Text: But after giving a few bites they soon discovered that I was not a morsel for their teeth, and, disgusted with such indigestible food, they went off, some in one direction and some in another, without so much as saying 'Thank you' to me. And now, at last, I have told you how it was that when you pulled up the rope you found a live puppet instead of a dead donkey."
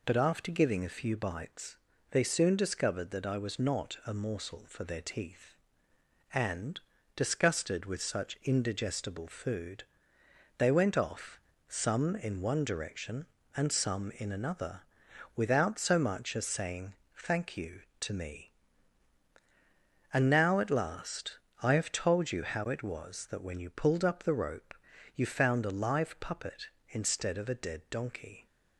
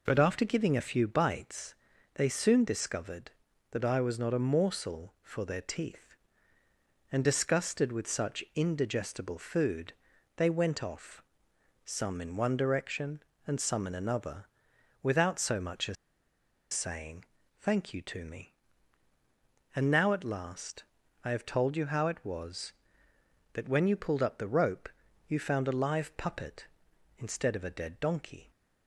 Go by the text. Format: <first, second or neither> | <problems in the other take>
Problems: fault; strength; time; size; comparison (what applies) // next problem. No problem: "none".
first | pauses between "bites" and "they"; at 1.7 s; 0.40 s long; slight in the first // pauses between "as" and "saying"; noticeable; at 15.9 s; 0.78 s long // pauses between "saying" and "Thank"; slight; at 17.2 s; 0.36 s long; slight in the first // pauses between "rope" and "you"; at 24.8 s; 0.40 s long; also in the first